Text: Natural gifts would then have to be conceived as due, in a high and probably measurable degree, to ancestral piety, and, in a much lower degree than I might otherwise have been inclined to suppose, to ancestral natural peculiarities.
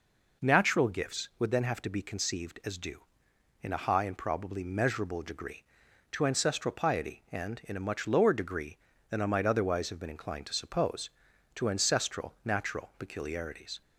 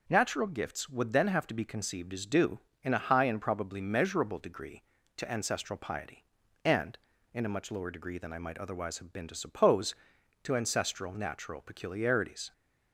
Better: first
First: none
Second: skips "inclined"; at 9.2 s

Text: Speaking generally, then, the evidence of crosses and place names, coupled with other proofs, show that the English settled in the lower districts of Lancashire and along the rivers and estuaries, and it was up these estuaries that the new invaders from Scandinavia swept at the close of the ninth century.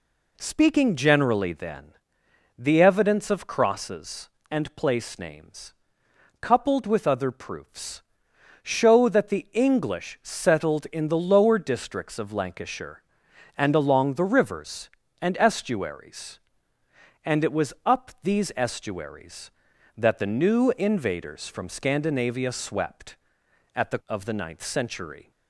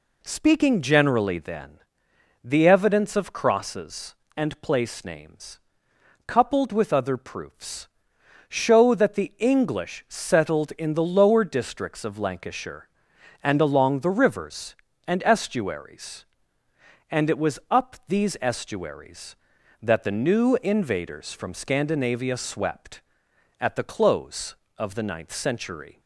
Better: second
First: skips "close"; at 24.0 s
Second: none

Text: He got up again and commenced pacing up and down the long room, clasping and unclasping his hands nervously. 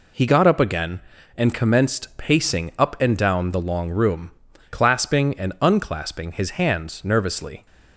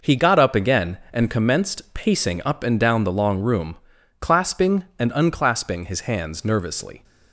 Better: neither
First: none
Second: none

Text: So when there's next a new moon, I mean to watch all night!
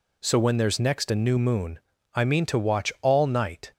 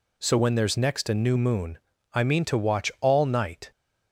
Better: neither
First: none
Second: none

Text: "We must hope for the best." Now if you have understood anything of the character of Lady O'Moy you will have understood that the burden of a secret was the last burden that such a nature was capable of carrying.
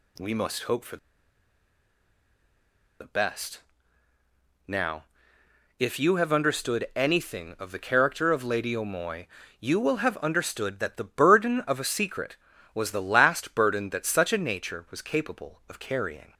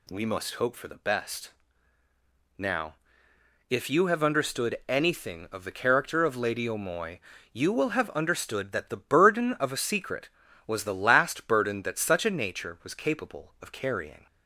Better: second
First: pauses between "for" and "the"; strong; at 0.9 s; 2.0 s long // pauses between "Now" and "if"; noticeable; at 5.0 s; 0.74 s long // pauses between "O'Moy" and "you"; slight; at 9.2 s; 0.32 s long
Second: pauses between "Now" and "if"; noticeable; at 2.9 s; 0.74 s long // pauses between "O'Moy" and "you"; slight; at 7.1 s; 0.32 s long

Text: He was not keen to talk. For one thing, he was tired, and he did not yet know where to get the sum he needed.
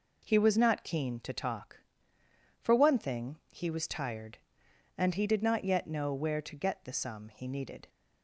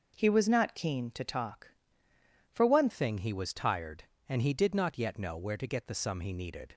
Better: first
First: none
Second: changes voice at "thing"; from 2.8 s on; 3.9 s long

